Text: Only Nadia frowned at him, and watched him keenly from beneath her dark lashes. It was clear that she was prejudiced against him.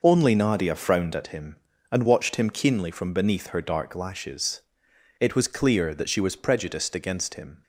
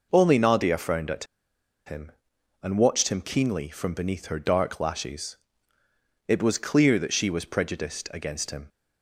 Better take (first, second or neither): first